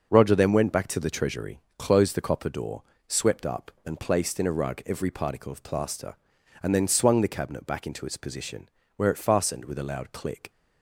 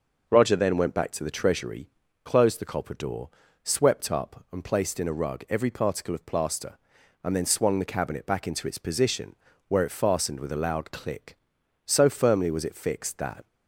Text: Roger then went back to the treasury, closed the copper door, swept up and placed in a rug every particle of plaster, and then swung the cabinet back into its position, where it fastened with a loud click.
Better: first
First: none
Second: goes on to say "So firmly was it fixed that"; from 11.8 s on; 1.6 s long

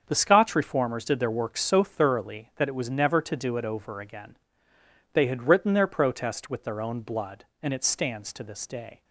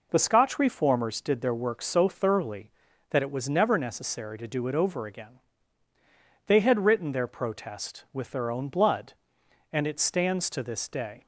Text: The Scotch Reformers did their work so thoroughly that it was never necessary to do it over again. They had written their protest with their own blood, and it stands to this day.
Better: second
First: starts louder than the rest; until 1.0 s; 7 dB // skips "necessary"; at 3.2 s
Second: none

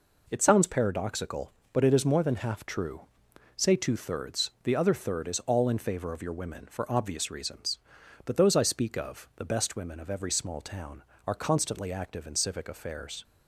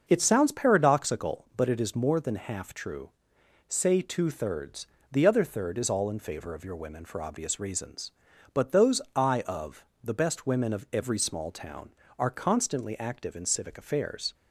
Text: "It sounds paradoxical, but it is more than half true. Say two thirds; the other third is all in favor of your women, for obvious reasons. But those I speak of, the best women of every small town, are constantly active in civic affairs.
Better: first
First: none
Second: starts louder than the rest; until 1.0 s; 6.5 dB // skips "speak"; at 9.4 s

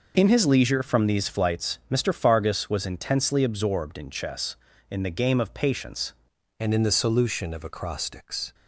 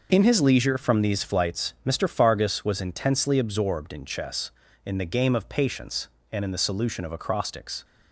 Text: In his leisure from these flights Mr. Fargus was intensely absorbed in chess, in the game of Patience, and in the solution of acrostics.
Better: second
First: changes voice at "and"; from 6.5 s on; 2.0 s long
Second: none

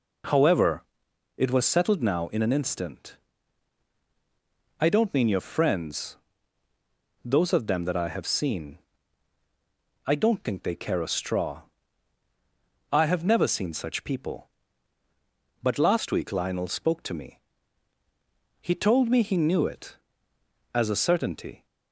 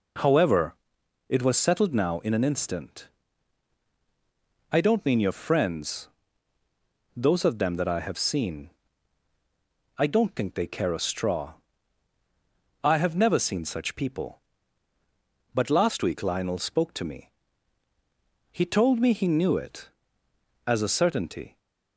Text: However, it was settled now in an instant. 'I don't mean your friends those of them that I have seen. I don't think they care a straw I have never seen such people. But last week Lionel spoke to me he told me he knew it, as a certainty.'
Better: neither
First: pauses between "friends" and "those"; at 6.1 s; 1.0 s long // pauses between "straw" and "I"; strong; at 11.6 s; 1.3 s long // pauses between "me" and "he"; at 17.3 s; 1.2 s long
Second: pauses between "friends" and "those"; at 6.0 s; 1.0 s long // pauses between "straw" and "I"; strong; at 11.5 s; 1.3 s long // pauses between "me" and "he"; at 17.2 s; 1.2 s long

